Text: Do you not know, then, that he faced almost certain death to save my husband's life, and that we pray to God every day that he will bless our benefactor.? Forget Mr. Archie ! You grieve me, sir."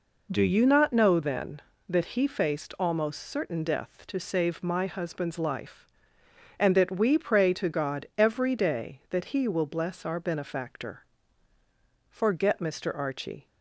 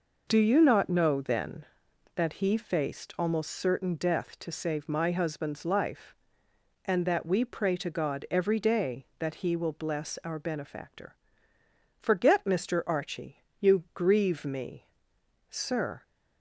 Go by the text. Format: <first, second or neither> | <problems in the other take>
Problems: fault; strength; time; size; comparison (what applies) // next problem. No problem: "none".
second | stops before "You grieve me sir"; at 13.4 s